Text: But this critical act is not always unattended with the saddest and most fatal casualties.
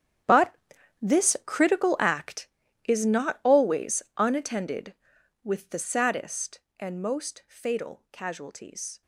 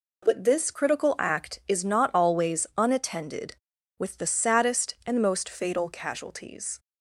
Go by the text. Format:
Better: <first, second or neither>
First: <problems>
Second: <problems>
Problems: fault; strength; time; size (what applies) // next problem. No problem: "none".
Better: second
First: gets quieter; strong; throughout; 17.5 dB // pauses between "But" and "this"; noticeable; at 0.5 s; 0.48 s long // pauses between "always" and "unattended"; slight; at 4.0 s; 0.16 s long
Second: none